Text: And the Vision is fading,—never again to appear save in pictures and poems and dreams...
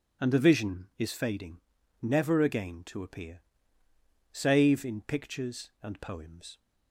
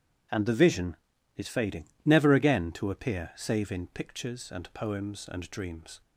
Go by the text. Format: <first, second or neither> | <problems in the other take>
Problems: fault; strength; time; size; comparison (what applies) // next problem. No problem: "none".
second | pauses between "appear" and "save"; noticeable; at 3.4 s; 0.90 s long // stops before "and dreams"; at 6.5 s